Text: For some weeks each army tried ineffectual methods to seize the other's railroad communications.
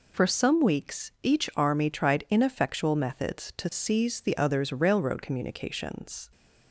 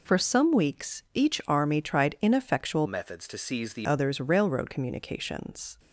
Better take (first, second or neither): first